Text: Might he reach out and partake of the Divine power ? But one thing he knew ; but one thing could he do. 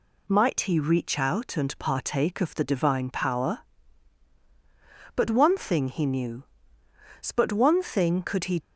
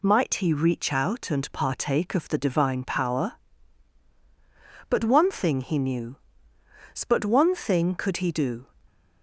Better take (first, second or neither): second